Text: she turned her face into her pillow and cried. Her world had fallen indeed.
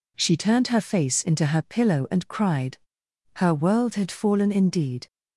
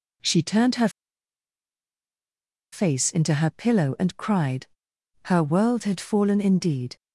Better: first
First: none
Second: pauses between "her" and "face"; strong; at 0.8 s; 1.8 s long

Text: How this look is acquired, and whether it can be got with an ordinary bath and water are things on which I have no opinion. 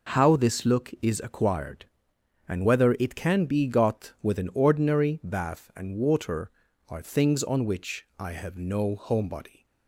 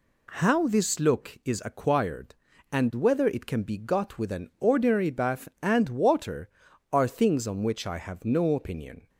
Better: second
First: says "homebody" for "opinion"; at 8.9 s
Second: none

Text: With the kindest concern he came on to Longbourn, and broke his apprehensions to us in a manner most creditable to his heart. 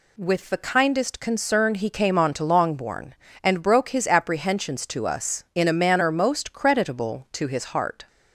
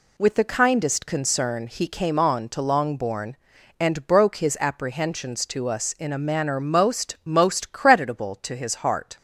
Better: first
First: none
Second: says "most" twice; at 7.2 s

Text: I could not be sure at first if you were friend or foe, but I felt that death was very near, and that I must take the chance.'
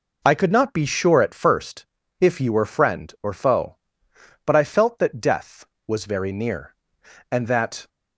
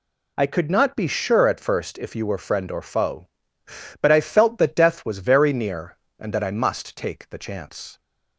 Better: second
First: pauses between "first" and "if"; slight; at 1.8 s; 0.36 s long // stops before "I must take the chance"; at 7.8 s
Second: none

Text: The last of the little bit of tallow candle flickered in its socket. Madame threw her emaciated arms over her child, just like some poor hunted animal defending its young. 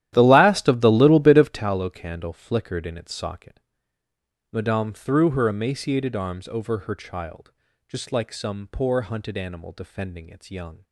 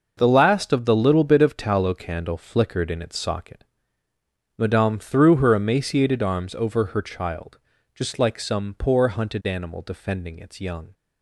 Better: second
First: starts louder than the rest; strong; until 1.7 s; 12.5 dB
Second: none

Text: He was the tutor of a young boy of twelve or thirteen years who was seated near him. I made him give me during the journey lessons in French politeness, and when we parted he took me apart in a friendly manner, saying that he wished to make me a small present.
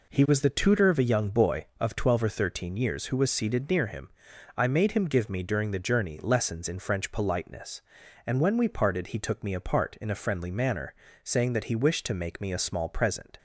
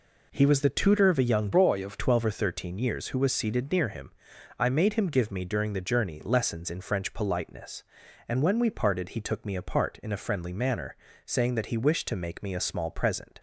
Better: first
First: none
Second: changes voice from "boy" to "of"; from 1.5 to 1.9 s; 0.4 s long

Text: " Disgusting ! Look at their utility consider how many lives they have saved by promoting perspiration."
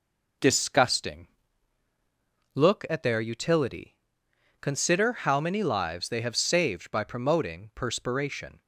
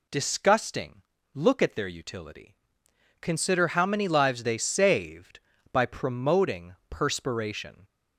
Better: first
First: pauses between "utility" and "consider"; noticeable; at 3.9 s; 0.64 s long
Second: pauses between "utility" and "consider"; noticeable; at 2.5 s; 0.64 s long // skips "have"; at 4.5 s

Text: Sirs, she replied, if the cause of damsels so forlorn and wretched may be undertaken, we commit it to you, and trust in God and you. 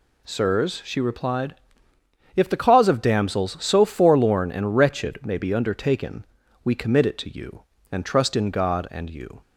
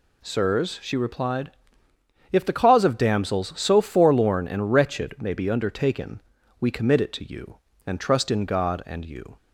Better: neither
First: none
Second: none

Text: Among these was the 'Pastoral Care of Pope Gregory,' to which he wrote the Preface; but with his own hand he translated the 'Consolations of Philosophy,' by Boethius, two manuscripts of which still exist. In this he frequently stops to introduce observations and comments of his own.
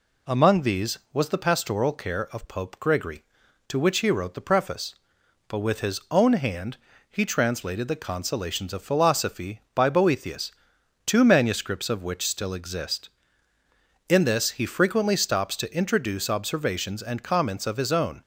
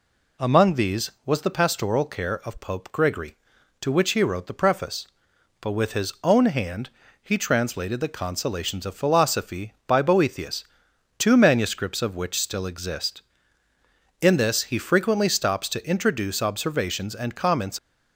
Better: first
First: pauses between "hand" and "he"; slight; at 6.7 s; 0.32 s long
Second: pauses between "hand" and "he"; slight; at 6.8 s; 0.32 s long // stops before "of his own"; at 17.7 s

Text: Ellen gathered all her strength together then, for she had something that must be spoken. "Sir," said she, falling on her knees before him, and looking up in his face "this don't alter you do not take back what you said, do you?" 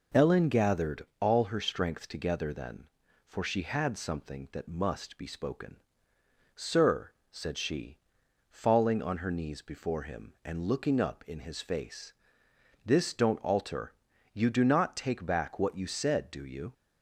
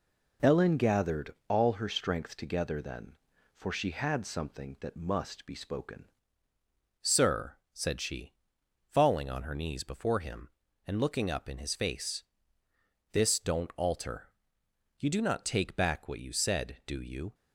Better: first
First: pauses between "face" and "this"; noticeable; at 12.1 s; 0.74 s long // pauses between "alter" and "you"; at 13.9 s; 0.40 s long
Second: changes voice at "Sir"; from 7.0 s on; 10.3 s long // pauses between "face" and "this"; noticeable; at 12.2 s; 0.88 s long // pauses between "alter" and "you"; noticeable; at 14.2 s; 0.72 s long

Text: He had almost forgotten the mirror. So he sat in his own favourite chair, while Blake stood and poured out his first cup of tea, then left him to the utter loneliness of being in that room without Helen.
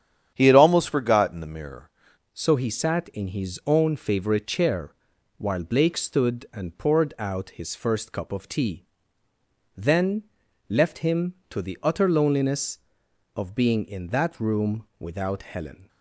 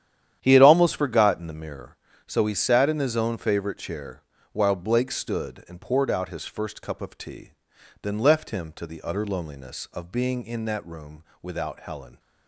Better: second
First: starts louder than the rest; strong; until 1.3 s; 9 dB // changes voice at "So"; from 2.3 s on; 13.5 s long // pauses between "then" and "left"; at 10.2 s; 0.44 s long // pauses between "room" and "without"; slight; at 14.8 s; 0.16 s long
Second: starts louder than the rest; strong; until 1.4 s; 10 dB // pauses between "room" and "without"; slight; at 11.2 s; 0.18 s long

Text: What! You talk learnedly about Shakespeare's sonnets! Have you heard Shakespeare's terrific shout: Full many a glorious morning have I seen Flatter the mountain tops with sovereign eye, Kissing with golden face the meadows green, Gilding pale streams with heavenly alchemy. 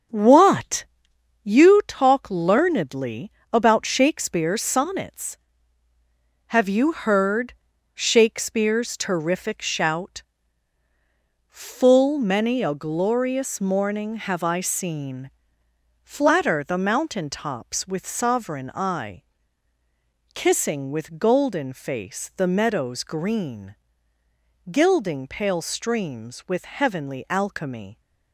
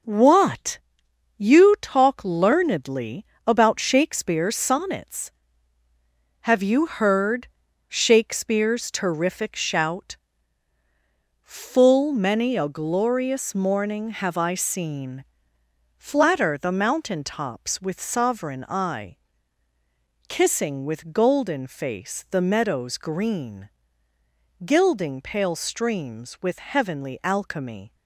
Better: second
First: starts louder than the rest; strong; until 1.4 s; 7.5 dB // pauses between "learnedly" and "about"; slight; at 3.2 s; 0.22 s long // pauses between "heard" and "Shakespeare's"; at 7.5 s; 0.40 s long // pauses between "seen" and "Flatter"; noticeable; at 15.2 s; 0.72 s long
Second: pauses between "learnedly" and "about"; slight; at 3.2 s; 0.22 s long // pauses between "heard" and "Shakespeare's"; at 7.4 s; 0.40 s long // pauses between "seen" and "Flatter"; noticeable; at 15.2 s; 0.72 s long

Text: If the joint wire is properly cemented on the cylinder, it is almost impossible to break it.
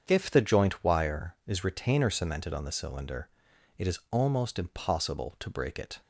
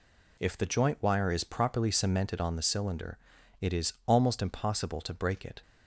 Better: second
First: starts louder than the rest; strong; until 1.0 s; 7.5 dB // says "retainer" for "properly"; at 1.6 s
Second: none

